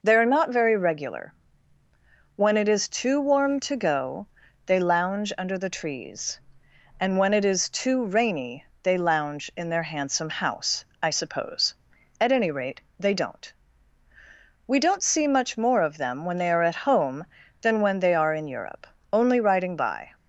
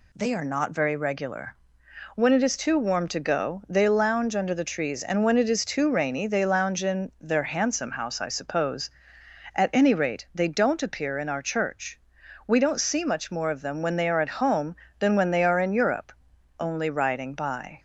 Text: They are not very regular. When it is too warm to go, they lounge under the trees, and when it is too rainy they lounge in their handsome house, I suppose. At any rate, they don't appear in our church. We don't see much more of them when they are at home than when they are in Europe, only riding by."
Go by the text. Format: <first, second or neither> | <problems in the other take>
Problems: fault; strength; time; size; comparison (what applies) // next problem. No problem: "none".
second | pauses between "rainy" and "they"; slight; at 8.6 s; 0.20 s long // skips "appear in our church"; at 14.0 s